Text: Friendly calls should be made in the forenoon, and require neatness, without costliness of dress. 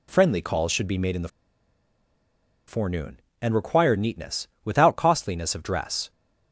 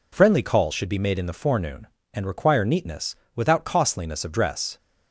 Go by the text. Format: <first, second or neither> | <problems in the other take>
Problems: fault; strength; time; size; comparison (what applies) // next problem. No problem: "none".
second | pauses between "the" and "forenoon"; strong; at 1.2 s; 1.4 s long